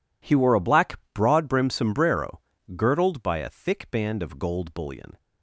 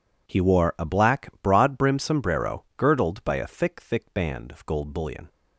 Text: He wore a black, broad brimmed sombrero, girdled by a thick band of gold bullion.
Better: first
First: none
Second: says "thick" twice; at 3.7 s

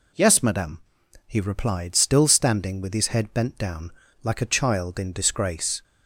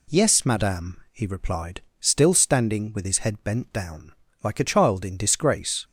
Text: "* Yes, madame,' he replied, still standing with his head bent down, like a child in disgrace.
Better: neither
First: none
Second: none

